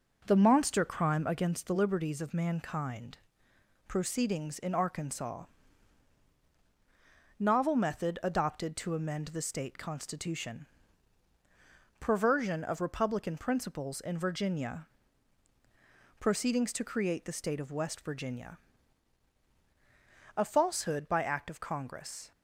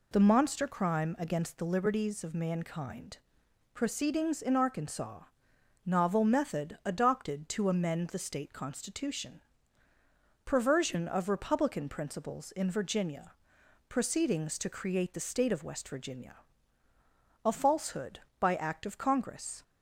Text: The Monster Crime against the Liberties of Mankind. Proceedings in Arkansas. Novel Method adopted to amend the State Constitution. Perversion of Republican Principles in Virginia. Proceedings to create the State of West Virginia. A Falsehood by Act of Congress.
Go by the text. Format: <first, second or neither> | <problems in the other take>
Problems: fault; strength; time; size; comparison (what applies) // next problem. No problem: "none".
second | starts louder than the rest; noticeable; until 1.5 s; 5.5 dB